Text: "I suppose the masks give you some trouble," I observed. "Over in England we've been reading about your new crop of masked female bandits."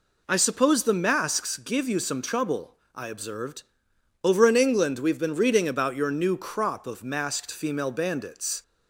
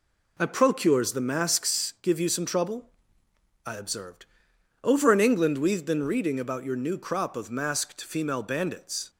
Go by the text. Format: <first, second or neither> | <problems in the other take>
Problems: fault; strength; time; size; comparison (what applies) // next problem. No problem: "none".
first | says "procures" for "suppose"; at 0.4 s